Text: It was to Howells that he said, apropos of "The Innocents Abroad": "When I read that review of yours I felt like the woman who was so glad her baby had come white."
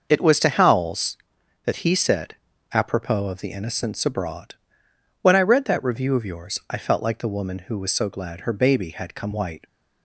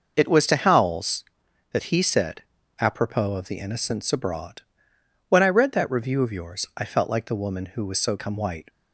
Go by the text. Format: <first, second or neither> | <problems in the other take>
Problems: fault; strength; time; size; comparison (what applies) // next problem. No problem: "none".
first | skips "glad her baby had"; at 8.1 s